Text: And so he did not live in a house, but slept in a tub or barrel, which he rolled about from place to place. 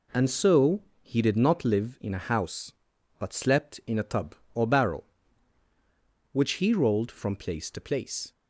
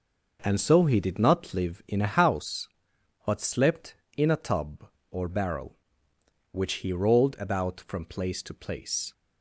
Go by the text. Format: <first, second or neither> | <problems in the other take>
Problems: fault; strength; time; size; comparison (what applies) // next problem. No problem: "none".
second | pauses between "so" and "he"; slight; at 0.8 s; 0.20 s long // skips "about"; at 7.1 s